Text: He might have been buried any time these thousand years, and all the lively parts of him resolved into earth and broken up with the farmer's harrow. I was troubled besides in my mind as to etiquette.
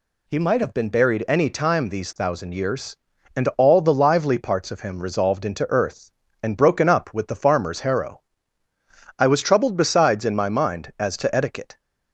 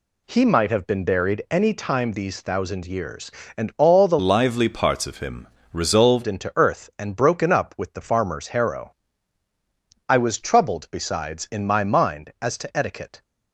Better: first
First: none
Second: changes voice from "lively" to "resolved"; from 4.1 to 6.2 s; 2.1 s long // pauses between "him" and "resolved"; slight; at 5.4 s; 0.24 s long

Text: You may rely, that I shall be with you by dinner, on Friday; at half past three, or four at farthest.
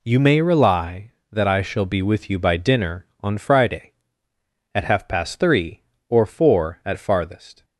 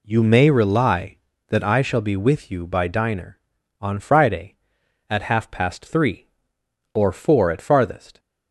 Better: first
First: none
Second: says "diner" for "dinner"; at 2.8 s

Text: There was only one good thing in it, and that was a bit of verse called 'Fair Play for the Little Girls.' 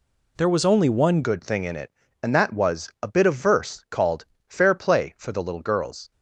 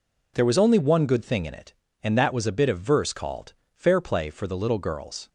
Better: second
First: changes voice at "good"; from 1.2 s on; 4.9 s long // pauses between "called" and "Fair"; slight; at 4.2 s; 0.24 s long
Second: pauses between "called" and "Fair"; slight; at 3.5 s; 0.22 s long

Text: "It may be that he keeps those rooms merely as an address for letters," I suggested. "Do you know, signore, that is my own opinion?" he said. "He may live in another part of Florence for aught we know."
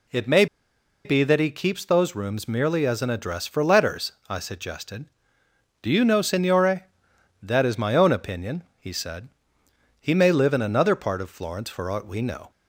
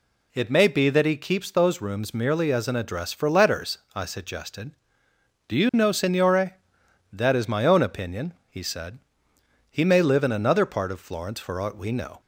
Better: second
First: pauses between "may" and "be"; noticeable; at 0.4 s; 0.59 s long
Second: none

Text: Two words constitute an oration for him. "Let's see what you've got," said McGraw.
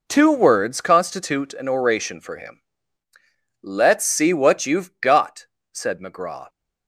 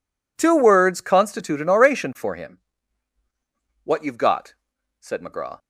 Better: first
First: none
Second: skips "Let's see"; at 3.2 s

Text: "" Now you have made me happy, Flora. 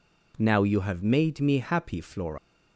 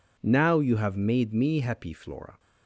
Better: second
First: leaves "Flora" unfinished; at 2.3 s; 110 ms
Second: none

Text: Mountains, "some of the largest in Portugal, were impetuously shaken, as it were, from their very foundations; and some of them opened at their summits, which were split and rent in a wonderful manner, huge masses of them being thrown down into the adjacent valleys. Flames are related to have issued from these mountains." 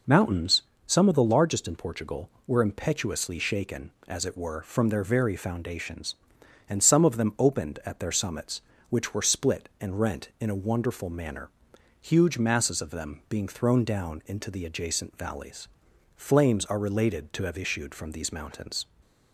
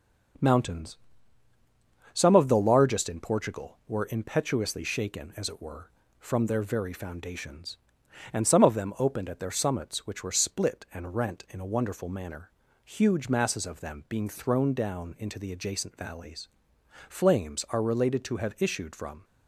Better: first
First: none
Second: stops before "these mountains"; at 19.2 s

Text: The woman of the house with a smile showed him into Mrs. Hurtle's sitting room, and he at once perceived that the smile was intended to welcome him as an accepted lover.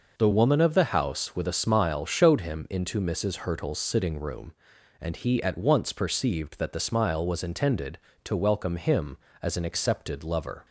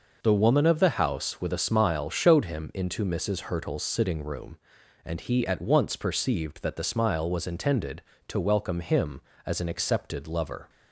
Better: neither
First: none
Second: none

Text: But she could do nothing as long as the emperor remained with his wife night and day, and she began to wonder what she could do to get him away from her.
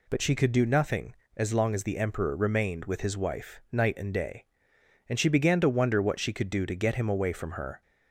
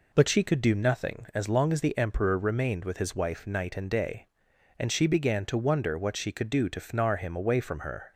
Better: first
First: none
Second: says "fnar" for "get"; at 6.8 s

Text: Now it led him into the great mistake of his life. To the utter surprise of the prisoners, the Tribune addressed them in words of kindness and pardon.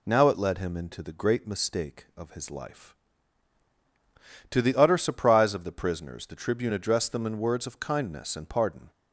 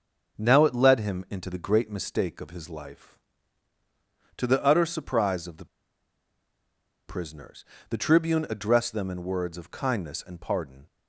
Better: first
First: none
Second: pauses between "the" and "prisoners"; strong; at 5.6 s; 1.4 s long

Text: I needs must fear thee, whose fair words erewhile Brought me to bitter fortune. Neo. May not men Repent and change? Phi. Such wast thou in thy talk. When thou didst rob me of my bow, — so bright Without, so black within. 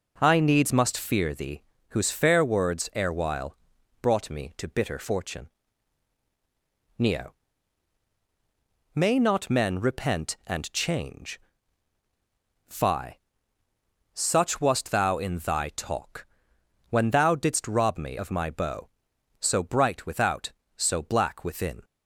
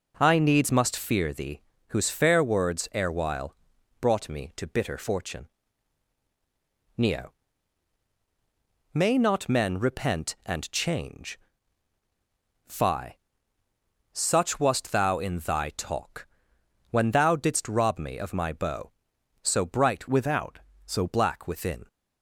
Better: first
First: pauses between "erewhile" and "Brought"; noticeable; at 3.5 s; 0.46 s long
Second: pauses between "erewhile" and "Brought"; noticeable; at 3.5 s; 0.46 s long // changes voice from "Without" to "so"; from 20.0 to 21.0 s; 1.0 s long

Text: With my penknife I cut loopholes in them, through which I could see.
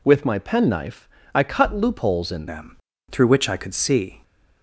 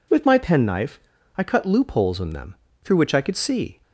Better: second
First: pauses between "penknife" and "I"; slight; at 1.0 s; 0.28 s long // changes voice at "them"; from 2.4 s on; 1.8 s long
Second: pauses between "penknife" and "I"; slight; at 1.0 s; 0.34 s long

